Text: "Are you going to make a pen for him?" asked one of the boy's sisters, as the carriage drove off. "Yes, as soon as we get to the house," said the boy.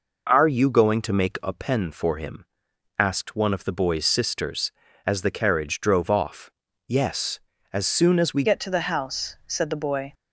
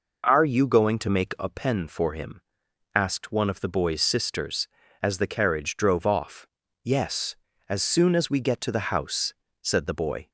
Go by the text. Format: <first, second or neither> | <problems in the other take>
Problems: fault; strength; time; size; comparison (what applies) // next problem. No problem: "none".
second | changes voice at "get"; from 8.4 s on; 1.7 s long